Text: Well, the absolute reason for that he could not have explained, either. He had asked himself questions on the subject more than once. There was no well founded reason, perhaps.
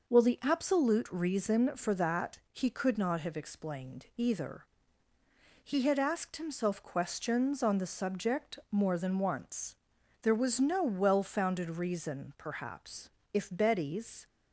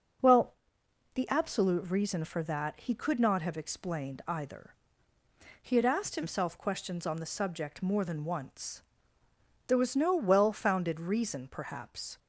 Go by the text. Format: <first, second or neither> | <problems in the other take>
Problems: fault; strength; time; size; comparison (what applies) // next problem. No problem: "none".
second | goes on to say "If Betty's"; noticeable; from 13.3 s on; 0.94 s long